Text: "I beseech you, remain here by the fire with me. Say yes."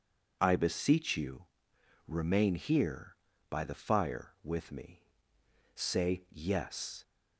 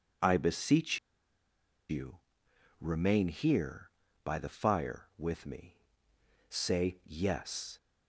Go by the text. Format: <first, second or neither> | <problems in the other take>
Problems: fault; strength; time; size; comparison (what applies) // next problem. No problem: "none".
first | pauses between "beseech" and "you"; noticeable; at 0.9 s; 0.91 s long